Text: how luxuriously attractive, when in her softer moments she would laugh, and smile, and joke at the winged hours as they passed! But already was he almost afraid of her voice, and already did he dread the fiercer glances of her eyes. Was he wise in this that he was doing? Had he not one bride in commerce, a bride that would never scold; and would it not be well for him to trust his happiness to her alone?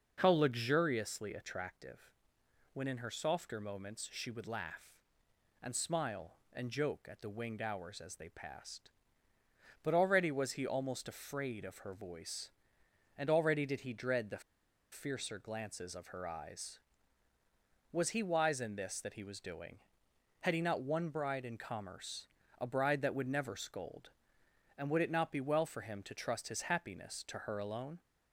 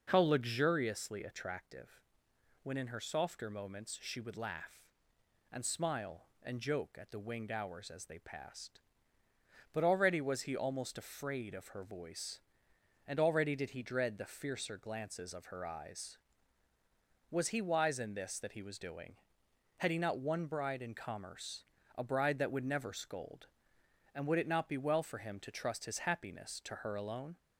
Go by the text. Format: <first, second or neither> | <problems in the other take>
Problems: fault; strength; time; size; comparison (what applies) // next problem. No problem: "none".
second | pauses between "the" and "fiercer"; noticeable; at 14.4 s; 0.51 s long